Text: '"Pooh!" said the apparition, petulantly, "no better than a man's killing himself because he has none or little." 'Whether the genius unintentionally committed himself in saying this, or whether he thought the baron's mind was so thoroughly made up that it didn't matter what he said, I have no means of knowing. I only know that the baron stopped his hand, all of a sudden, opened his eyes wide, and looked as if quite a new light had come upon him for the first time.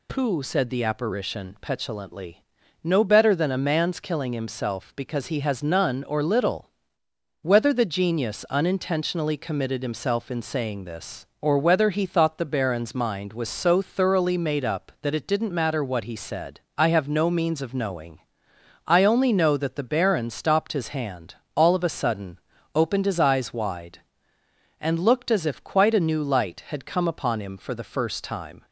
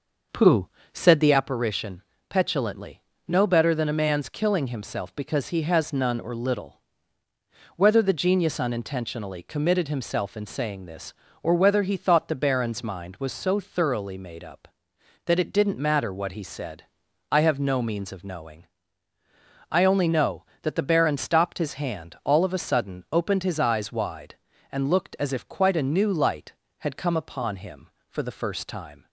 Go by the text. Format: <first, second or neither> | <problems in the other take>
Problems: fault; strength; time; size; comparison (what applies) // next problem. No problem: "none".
first | starts louder than the rest; noticeable; until 1.4 s; 6 dB